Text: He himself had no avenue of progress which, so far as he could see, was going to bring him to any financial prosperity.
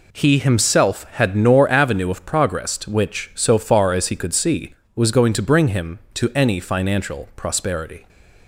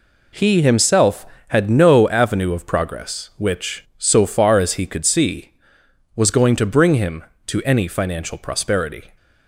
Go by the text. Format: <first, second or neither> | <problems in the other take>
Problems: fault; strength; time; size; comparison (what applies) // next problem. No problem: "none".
second | says "nor" for "no"; at 1.3 s